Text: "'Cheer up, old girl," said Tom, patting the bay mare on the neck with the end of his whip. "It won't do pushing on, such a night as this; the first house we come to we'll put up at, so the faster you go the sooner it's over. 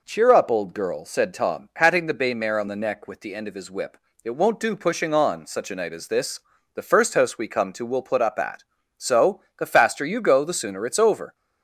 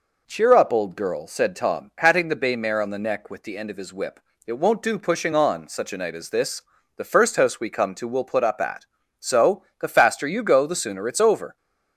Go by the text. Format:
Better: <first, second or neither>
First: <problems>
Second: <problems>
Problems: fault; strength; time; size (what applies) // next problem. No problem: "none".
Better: neither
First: pauses between "so" and "the"; slight; at 9.4 s; 0.18 s long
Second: pauses between "so" and "the"; slight; at 9.6 s; 0.18 s long